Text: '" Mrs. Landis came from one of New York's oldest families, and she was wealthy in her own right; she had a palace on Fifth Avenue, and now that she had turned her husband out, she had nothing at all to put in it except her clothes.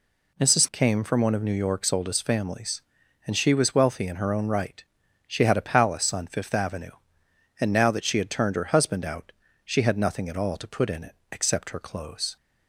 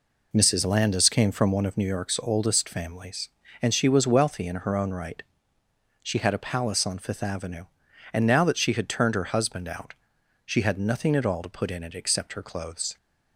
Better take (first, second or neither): second